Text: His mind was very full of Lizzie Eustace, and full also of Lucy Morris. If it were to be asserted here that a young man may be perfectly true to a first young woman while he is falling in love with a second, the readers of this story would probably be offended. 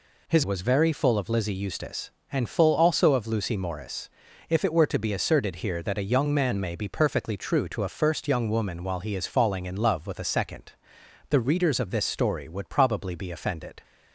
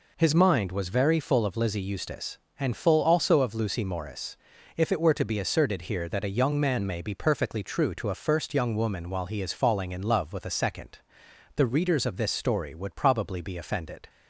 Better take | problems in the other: second | skips "mind"; at 0.4 s

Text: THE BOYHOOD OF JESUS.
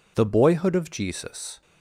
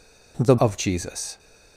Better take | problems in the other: first | skips "BOYHOOD"; at 0.5 s

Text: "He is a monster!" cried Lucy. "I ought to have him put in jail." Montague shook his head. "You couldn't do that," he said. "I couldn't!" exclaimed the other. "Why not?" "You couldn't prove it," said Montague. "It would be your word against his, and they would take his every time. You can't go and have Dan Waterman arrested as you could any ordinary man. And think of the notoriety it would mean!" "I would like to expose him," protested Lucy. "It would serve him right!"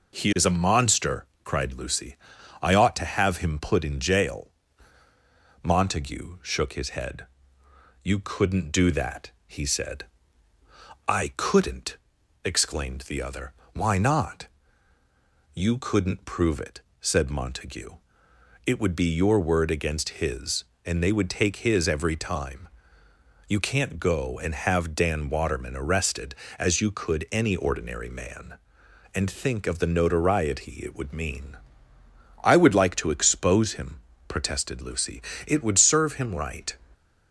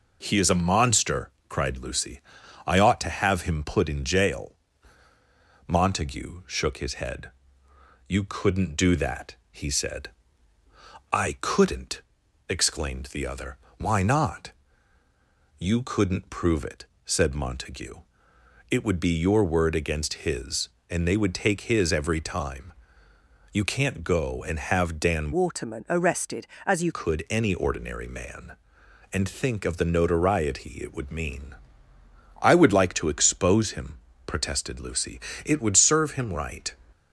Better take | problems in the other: first | changes voice from "Waterman" to "you"; from 25.3 to 26.9 s; 1.6 s long

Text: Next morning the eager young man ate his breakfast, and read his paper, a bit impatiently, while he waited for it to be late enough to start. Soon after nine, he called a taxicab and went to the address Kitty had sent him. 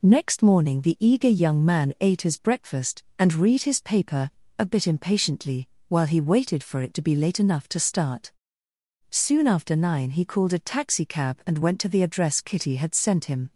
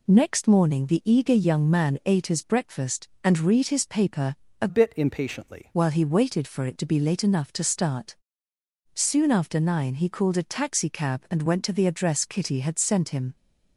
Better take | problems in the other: first | changes voice from "bit" to "impatiently"; from 4.6 to 5.7 s; 1.1 s long

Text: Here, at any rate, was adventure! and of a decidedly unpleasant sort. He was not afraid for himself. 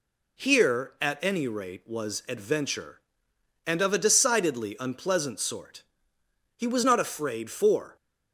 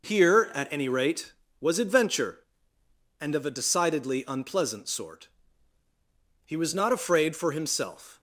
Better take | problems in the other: second | stops before "himself"; at 7.9 s

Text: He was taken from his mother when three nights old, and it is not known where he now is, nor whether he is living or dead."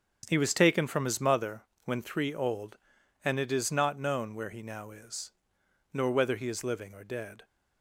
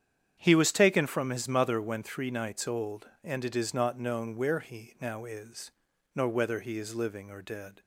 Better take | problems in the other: second | starts louder than the rest; strong; until 1.3 s; 7.5 dB; strong in the second // pauses between "mother" and "when"; slight; at 1.6 s; 0.20 s long // skips "nights"; at 2.3 s

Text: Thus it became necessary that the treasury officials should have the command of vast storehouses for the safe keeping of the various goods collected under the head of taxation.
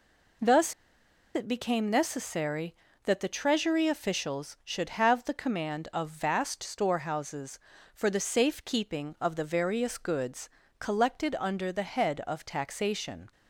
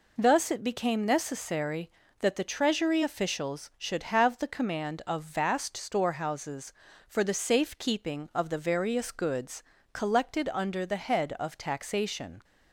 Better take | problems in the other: second | pauses between "Thus" and "it"; noticeable; at 0.7 s; 0.61 s long // pauses between "goods" and "collected"; slight; at 10.4 s; 0.30 s long; slight in the second

